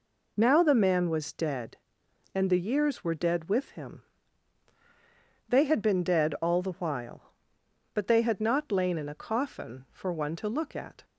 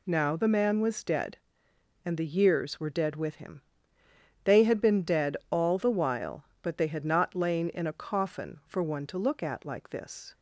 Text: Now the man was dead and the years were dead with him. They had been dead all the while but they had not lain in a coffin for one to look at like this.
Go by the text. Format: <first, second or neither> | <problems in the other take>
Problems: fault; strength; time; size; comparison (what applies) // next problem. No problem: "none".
second | stops before "like this"; at 11.0 s